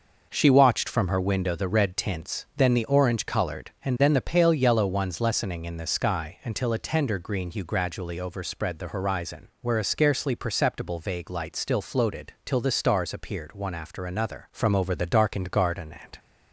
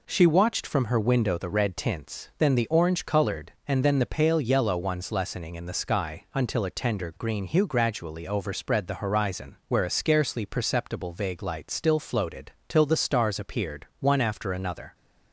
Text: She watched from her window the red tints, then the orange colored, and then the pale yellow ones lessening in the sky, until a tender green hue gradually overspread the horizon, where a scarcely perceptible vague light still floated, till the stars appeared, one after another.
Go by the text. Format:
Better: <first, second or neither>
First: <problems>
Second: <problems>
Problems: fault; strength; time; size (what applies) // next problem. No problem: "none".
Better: second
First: goes on to say "From over the darkened garden and"; from 14.5 s on; 1.6 s long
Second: none